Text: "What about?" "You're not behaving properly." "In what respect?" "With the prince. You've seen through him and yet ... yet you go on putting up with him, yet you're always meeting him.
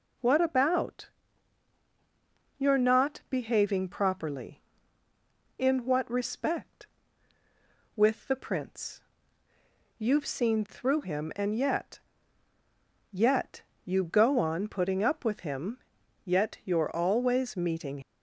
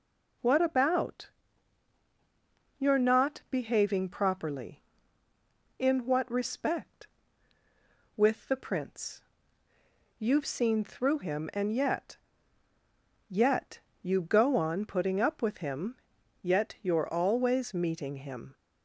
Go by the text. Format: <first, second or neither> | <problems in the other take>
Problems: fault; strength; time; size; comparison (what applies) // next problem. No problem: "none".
second | pauses between "yet" and "you"; slight; at 13.6 s; 0.24 s long; slight in the second // stops before "him"; at 18.0 s